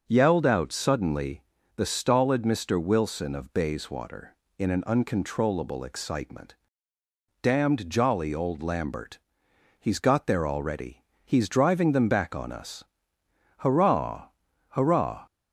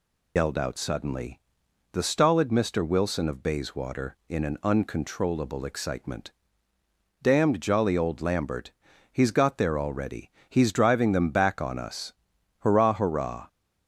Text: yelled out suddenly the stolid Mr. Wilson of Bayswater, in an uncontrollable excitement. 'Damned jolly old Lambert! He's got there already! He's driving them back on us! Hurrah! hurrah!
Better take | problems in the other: first | loses the start of "yelled"; at 0.3 s; 105 ms // pauses between "suddenly" and "the"; noticeable; at 1.3 s; 0.52 s long; slight in the first

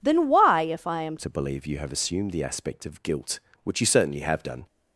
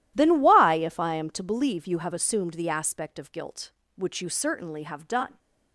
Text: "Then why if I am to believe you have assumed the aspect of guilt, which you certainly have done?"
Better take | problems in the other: second | changes voice at "to"; from 1.1 s on; 3.5 s long

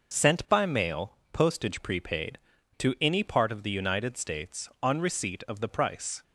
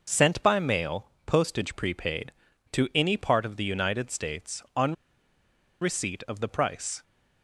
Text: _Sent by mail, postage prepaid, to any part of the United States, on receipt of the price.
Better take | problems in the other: first | pauses between "on" and "receipt"; noticeable; at 4.9 s; 0.87 s long

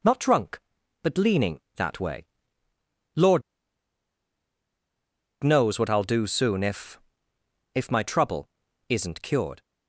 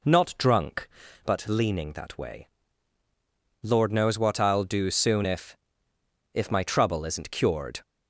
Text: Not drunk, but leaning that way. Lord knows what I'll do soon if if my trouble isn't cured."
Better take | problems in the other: second | pauses between "Lord" and "knows"; strong; at 3.4 s; 1.9 s long // pauses between "if" and "if"; noticeable; at 6.9 s; 0.74 s long; noticeable in the second // pauses between "trouble" and "isn't"; at 8.4 s; 0.40 s long

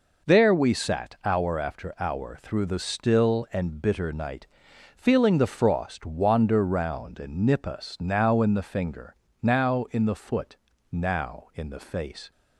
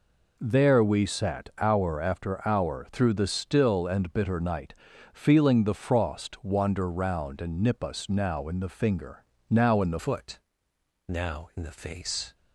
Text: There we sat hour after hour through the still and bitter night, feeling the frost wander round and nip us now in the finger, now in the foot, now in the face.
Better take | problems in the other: first | changes voice at "foot"; from 9.9 s on; 2.4 s long

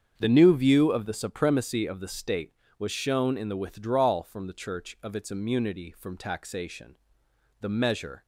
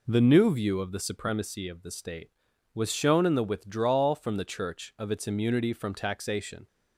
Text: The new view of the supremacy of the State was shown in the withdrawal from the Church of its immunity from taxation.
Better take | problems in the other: second | starts louder than the rest; strong; until 1.2 s; 7 dB // goes on to say "The measure"; noticeable; from 7.5 s on; 0.66 s long

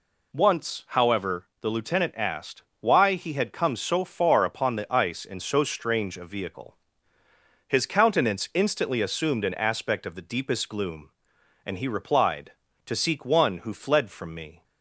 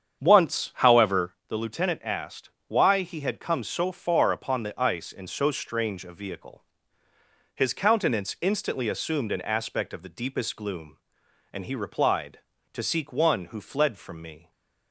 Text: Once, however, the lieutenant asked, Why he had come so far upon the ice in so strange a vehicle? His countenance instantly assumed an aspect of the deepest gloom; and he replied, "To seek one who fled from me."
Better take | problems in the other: first | starts louder than the rest; strong; until 1.5 s; 8 dB // stays silent after the last word; slight; from 14.3 s on; 0.6 s long

